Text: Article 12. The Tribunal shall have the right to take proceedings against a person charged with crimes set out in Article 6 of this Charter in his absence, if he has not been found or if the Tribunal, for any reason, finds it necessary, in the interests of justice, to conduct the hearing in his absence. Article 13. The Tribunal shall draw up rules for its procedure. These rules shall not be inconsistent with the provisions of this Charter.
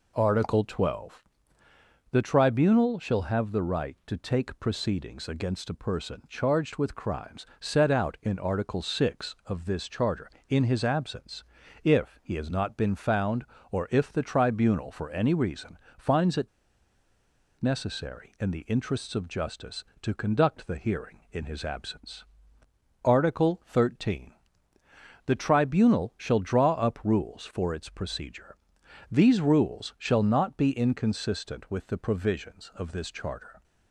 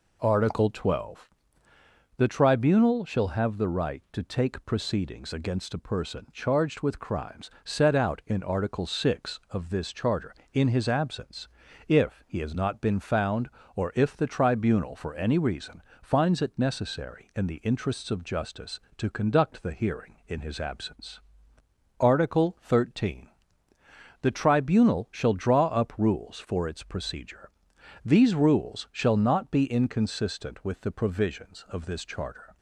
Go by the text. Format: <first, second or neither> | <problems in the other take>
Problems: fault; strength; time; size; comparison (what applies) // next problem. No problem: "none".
second | pauses between "it" and "necessary"; at 16.4 s; 1.1 s long